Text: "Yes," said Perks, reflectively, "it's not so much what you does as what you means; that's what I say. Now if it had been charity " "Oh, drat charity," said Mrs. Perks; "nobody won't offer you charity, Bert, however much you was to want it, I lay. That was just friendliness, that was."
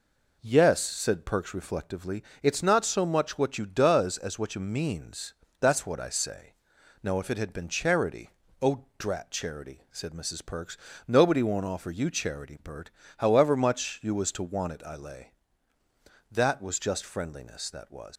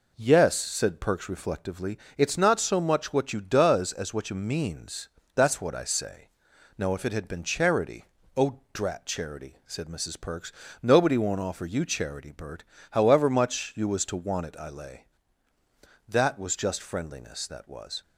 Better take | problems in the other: second | leaves "was" unfinished; at 18.1 s; 90 ms

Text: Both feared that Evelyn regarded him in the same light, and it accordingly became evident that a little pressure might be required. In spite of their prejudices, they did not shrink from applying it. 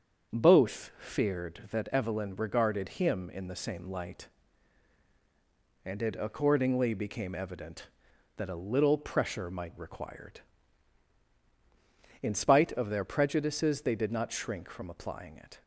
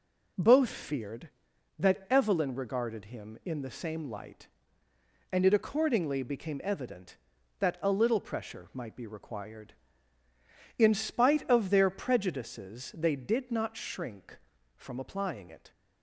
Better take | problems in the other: second | starts louder than the rest; until 1.4 s; 7 dB // skips "be"; at 9.7 s

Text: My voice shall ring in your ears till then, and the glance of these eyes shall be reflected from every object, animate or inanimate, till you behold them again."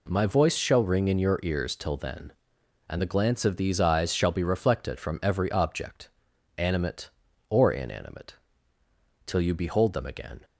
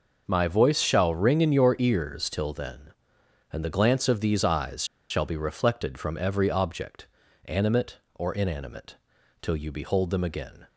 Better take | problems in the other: first | pauses between "eyes" and "shall"; slight; at 4.8 s; 0.25 s long

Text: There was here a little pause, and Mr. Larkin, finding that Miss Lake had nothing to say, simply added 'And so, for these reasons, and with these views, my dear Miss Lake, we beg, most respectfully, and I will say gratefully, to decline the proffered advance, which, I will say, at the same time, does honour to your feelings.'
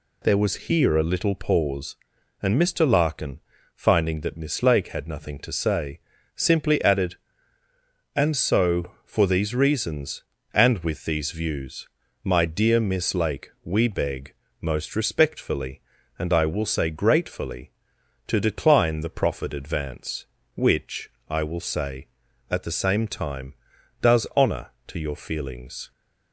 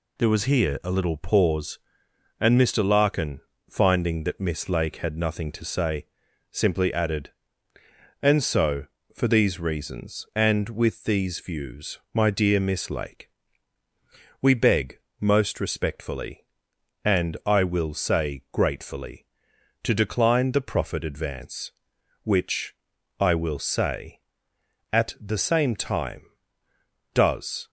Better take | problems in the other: first | stops before "honour to your feelings"; at 27.6 s

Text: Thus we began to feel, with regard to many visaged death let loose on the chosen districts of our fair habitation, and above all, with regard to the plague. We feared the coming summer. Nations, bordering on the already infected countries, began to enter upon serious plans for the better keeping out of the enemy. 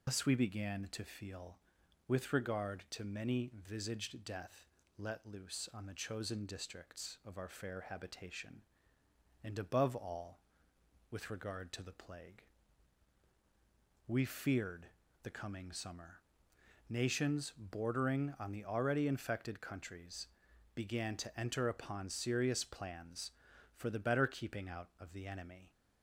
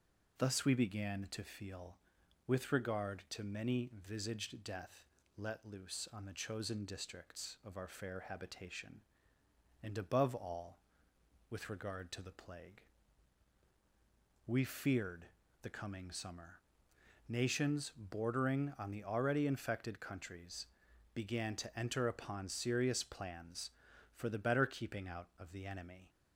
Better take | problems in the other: second | loses the start of "Thus"; at 0.0 s; 85 ms // pauses between "death" and "let"; slight; at 4.6 s; 0.32 s long; slight in the second // pauses between "feared" and "the"; slight; at 14.8 s; 0.36 s long; slight in the second

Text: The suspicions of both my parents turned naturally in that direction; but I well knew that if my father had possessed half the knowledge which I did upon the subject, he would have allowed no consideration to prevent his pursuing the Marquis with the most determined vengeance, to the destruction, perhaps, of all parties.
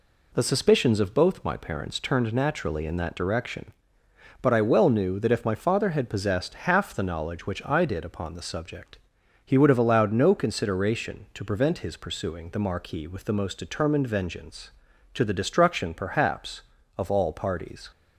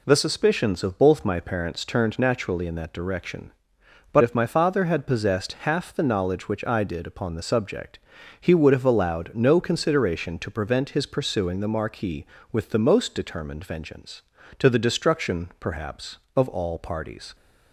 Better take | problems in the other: first | skips "I well knew that"; at 4.2 s

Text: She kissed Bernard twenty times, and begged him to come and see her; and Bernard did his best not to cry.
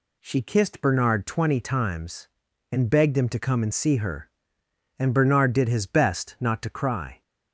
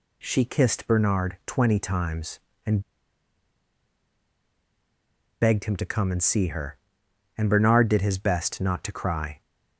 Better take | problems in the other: first | pauses between "and" and "begged"; strong; at 2.7 s; 2.6 s long

